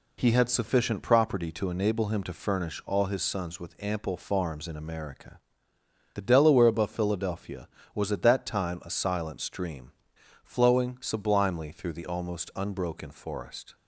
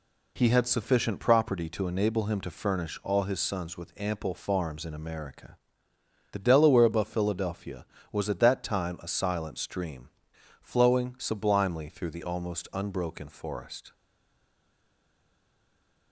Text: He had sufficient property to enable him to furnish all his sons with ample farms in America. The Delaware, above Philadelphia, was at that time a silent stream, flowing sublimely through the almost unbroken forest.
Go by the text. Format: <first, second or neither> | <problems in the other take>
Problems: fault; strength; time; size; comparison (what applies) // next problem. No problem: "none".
first | stays silent after the last word; from 13.9 s on; 2.2 s long